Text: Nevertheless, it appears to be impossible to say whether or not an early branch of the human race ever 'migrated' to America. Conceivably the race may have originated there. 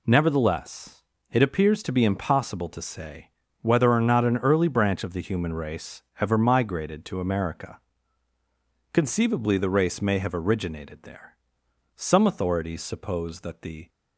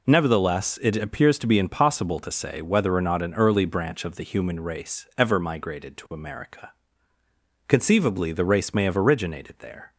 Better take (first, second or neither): second